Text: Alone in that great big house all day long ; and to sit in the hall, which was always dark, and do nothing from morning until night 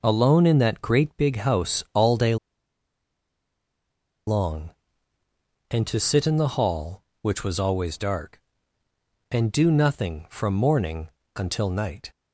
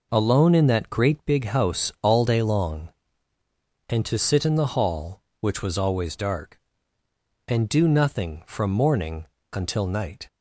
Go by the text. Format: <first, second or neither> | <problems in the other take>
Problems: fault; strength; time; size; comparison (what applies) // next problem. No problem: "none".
second | pauses between "day" and "long"; strong; at 2.3 s; 1.9 s long // pauses between "morning" and "until"; slight; at 11.1 s; 0.26 s long; slight in the second